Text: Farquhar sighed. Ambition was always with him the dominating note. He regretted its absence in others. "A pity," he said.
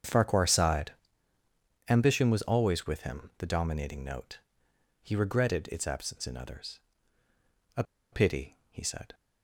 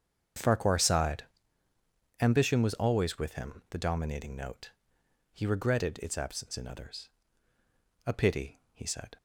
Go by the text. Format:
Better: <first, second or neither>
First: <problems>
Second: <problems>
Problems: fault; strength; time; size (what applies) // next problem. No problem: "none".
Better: second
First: starts louder than the rest; strong; until 2.0 s; 7.5 dB // pauses between "A" and "pity"; slight; at 7.8 s; 0.29 s long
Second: starts louder than the rest; strong; until 2.3 s; 7.5 dB